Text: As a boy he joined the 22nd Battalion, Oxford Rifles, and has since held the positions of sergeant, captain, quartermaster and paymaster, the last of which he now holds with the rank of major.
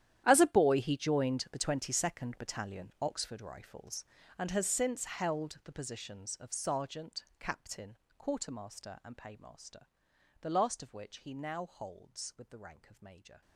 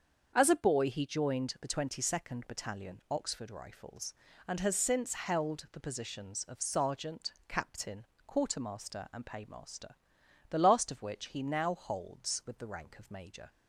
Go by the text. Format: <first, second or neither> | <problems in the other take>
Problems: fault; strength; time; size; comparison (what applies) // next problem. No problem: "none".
second | gets quieter; strong; throughout; 18 dB // starts louder than the rest; strong; until 1.2 s; 11 dB; also in the second